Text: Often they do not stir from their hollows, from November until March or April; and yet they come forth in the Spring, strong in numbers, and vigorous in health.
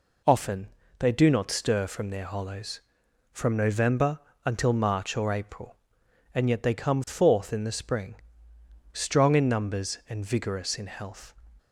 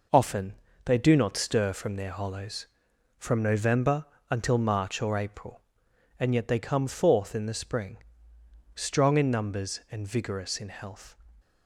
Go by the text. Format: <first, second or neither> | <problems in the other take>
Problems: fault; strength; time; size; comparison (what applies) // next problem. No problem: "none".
first | gets quieter; throughout; 6.5 dB // pauses between "Often" and "they"; slight; at 0.5 s; 0.30 s long; slight in the first // pauses between "November" and "until"; slight; at 4.0 s; 0.23 s long; slight in the first